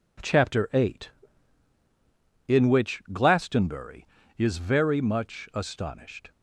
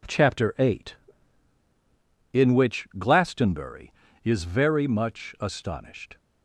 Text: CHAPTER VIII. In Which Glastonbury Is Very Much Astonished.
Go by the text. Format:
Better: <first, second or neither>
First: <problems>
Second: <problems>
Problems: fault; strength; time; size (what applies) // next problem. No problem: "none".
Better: neither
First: none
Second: none